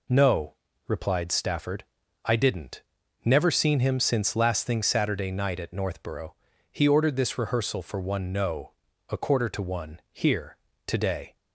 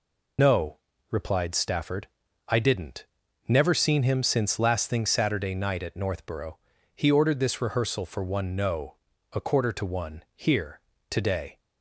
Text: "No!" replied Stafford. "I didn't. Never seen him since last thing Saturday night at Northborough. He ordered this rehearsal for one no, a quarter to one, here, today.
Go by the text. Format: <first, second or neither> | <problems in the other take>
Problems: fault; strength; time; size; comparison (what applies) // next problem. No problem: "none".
first | loses the start of "No"; at 0.3 s; 60 ms